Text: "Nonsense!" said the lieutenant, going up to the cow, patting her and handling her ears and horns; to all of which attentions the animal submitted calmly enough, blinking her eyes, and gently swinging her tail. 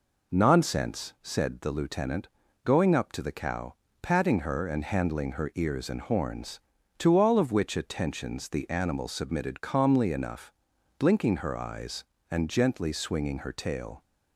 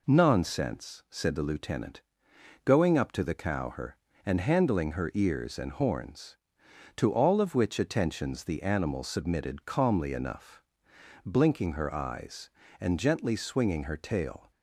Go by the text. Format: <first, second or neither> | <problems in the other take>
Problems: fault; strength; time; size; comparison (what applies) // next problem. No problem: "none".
first | skips "patting"; at 3.7 s